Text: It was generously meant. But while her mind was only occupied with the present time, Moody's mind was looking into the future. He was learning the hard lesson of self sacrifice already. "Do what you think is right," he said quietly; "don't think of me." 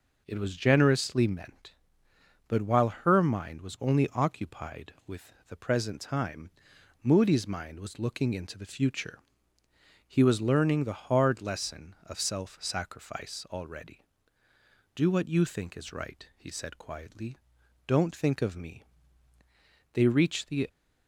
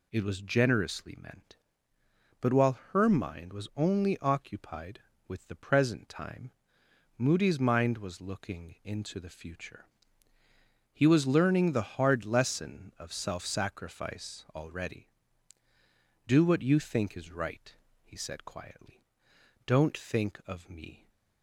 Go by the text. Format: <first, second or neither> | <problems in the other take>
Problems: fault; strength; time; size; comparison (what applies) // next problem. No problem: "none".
second | pauses between "with" and "the"; slight; at 5.3 s; 0.16 s long // goes on to say "They reached the"; noticeable; from 19.9 s on; 0.74 s long